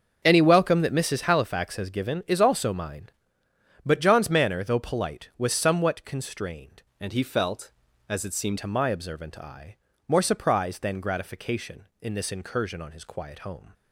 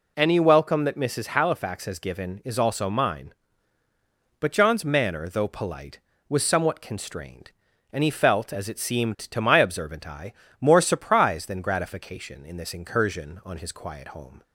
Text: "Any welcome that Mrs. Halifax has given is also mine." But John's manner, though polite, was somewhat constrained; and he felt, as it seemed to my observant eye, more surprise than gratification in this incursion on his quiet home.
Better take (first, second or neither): second